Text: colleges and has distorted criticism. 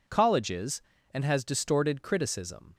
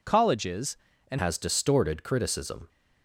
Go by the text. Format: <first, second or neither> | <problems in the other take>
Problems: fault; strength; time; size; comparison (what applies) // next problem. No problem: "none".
first | changes voice at "has"; from 1.1 s on; 1.5 s long